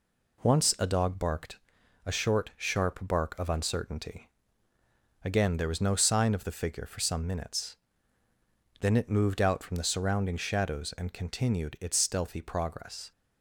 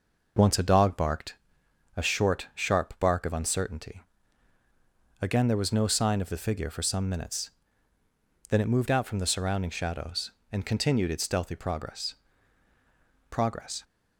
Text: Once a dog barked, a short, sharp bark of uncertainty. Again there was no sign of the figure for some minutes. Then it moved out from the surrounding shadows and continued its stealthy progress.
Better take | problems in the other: first | says "progress" twice; at 13.3 s

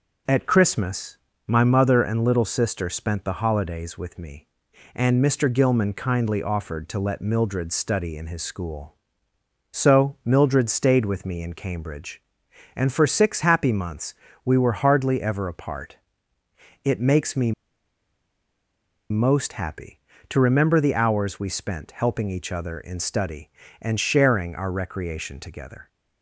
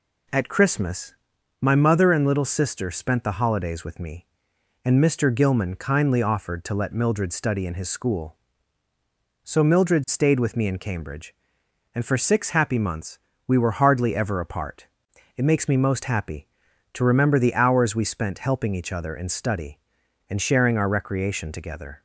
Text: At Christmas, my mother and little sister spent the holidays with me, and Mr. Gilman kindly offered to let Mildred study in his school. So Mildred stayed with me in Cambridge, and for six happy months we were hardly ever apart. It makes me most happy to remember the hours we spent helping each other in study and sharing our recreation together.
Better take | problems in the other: second | pauses between "months" and "we"; slight; at 14.1 s; 0.28 s long; slight in the second // pauses between "me" and "most"; strong; at 17.5 s; 1.5 s long

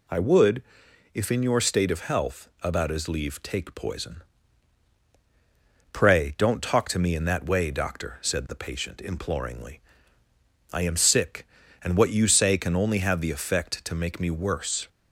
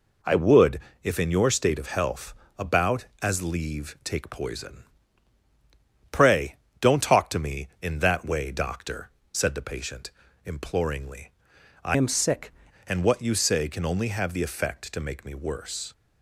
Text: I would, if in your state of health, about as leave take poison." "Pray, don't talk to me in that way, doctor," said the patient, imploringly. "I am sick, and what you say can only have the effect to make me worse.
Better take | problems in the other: first | changes voice from "am" to "sick"; from 11.9 to 12.5 s; 0.6 s long

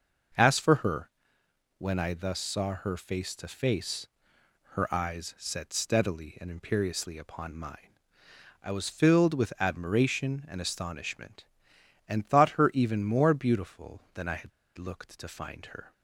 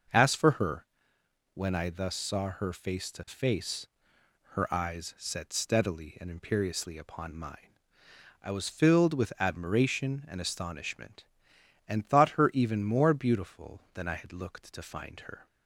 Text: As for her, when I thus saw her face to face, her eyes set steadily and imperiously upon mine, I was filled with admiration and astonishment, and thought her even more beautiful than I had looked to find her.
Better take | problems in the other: second | starts louder than the rest; noticeable; until 2.0 s; 6 dB; noticeable in the second // pauses between "had" and "looked"; slight; at 14.5 s; 0.28 s long

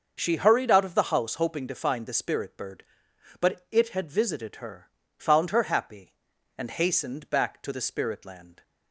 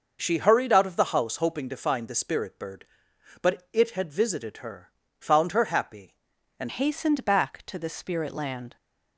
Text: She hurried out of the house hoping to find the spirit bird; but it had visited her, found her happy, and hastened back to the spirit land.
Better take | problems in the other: first | starts louder than the rest; noticeable; until 1.2 s; 6 dB; also in the first // changes voice at "hastened"; from 6.6 s on; 2.1 s long

